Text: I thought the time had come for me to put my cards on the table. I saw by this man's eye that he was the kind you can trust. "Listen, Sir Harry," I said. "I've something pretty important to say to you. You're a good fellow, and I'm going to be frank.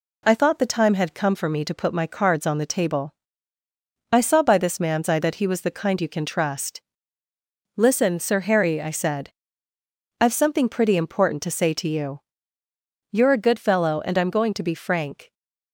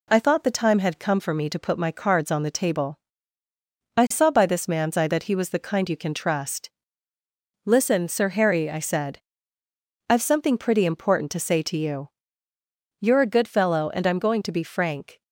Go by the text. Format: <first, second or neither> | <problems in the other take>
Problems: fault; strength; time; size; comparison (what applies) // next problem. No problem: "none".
neither | none